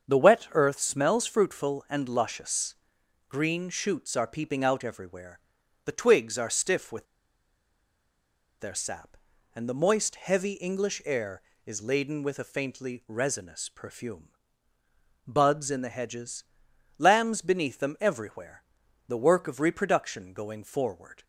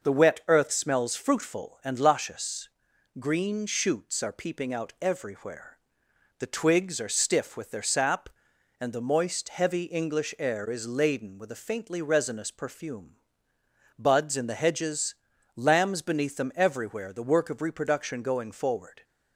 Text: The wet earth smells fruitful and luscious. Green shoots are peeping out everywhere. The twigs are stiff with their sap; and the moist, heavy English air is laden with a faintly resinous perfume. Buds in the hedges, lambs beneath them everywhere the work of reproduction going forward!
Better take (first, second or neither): second